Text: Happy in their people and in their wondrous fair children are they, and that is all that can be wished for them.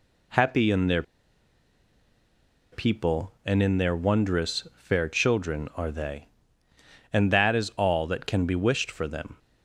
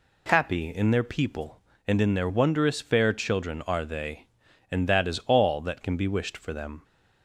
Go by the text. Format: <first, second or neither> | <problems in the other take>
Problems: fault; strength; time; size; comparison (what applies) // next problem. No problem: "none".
second | pauses between "their" and "people"; strong; at 1.0 s; 1.6 s long